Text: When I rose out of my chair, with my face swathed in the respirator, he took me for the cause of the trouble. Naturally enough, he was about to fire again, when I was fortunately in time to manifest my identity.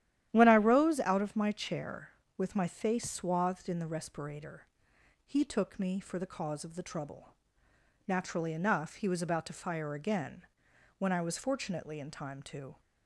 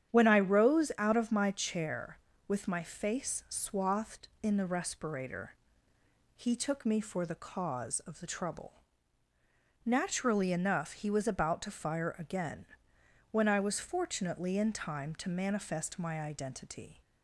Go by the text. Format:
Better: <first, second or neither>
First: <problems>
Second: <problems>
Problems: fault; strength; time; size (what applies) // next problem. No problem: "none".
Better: second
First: starts louder than the rest; strong; until 1.3 s; 11.5 dB // stops before "manifest my identity"; at 12.7 s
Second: starts louder than the rest; strong; until 1.1 s; 9.5 dB